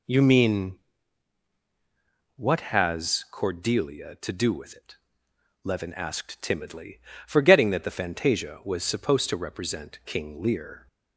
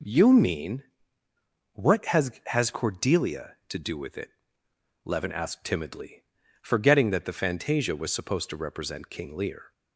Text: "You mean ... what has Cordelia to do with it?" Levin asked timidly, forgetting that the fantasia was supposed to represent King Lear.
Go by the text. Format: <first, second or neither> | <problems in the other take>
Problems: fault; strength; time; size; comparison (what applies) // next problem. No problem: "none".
first | says "has" twice; at 2.4 s